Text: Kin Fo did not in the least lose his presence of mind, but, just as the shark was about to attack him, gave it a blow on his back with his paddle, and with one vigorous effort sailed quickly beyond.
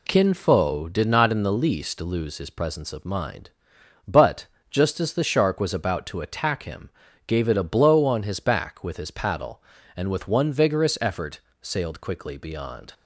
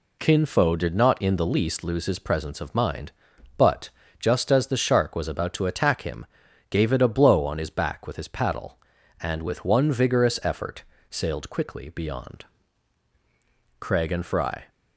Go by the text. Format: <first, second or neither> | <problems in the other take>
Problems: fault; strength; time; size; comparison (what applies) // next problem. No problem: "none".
first | pauses between "effort" and "sailed"; slight; at 10.8 s; 0.26 s long; slight in the first // goes on to say "Craig and Fry"; noticeable; from 13.8 s on; 0.88 s long